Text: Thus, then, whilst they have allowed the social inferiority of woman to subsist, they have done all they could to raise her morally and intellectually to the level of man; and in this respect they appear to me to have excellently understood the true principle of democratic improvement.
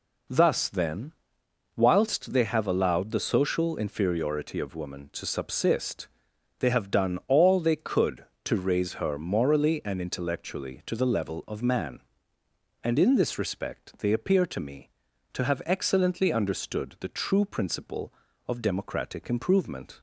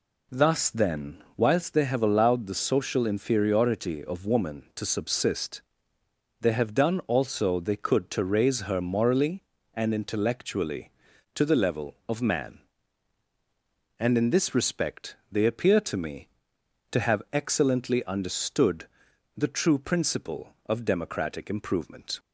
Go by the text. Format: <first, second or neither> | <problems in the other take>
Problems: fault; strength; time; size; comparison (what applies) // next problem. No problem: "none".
first | says "also" for "all"; at 7.0 s // pauses between "respect" and "they"; slight; at 15.1 s; 0.16 s long // pauses between "understood" and "the"; noticeable; at 18.8 s; 0.50 s long